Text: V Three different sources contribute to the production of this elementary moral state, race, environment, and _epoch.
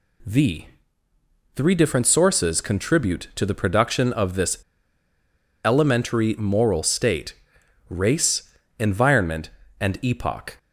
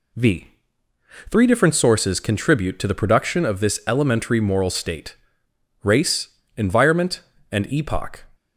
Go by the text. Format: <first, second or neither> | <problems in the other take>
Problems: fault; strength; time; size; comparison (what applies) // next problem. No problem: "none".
second | pauses between "V" and "Three"; noticeable; at 0.6 s; 0.88 s long; noticeable in the second // pauses between "this" and "elementary"; at 4.5 s; 1.0 s long